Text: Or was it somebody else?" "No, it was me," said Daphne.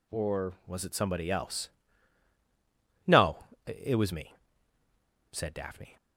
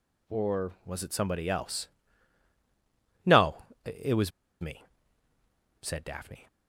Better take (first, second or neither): first